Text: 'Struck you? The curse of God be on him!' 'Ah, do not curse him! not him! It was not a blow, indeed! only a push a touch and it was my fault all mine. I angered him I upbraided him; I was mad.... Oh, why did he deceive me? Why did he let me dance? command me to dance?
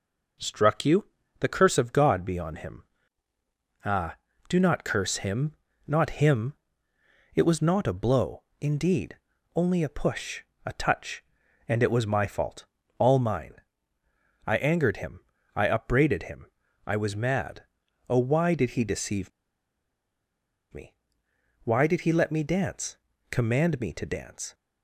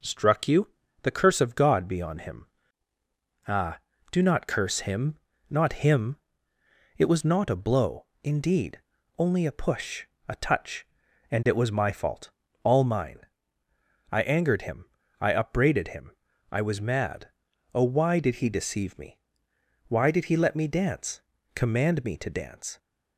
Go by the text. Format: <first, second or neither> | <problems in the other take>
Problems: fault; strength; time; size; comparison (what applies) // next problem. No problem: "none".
second | pauses between "push" and "a"; slight; at 10.4 s; 0.22 s long; slight in the second // pauses between "fault" and "all"; slight; at 12.6 s; 0.36 s long; slight in the second // pauses between "him" and "I"; at 15.1 s; 0.38 s long; also in the second // pauses between "deceive" and "me"; strong; at 19.3 s; 1.4 s long